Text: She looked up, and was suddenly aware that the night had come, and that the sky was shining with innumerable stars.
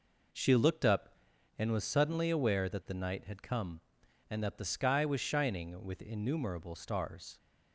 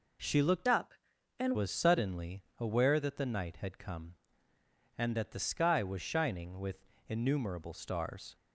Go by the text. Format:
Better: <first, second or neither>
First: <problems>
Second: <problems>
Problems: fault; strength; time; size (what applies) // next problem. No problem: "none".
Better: first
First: none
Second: changes voice from "up" to "and"; from 0.6 to 1.5 s; 0.9 s long // pauses between "suddenly" and "aware"; slight; at 2.4 s; 0.16 s long // pauses between "with" and "innumerable"; slight; at 6.8 s; 0.20 s long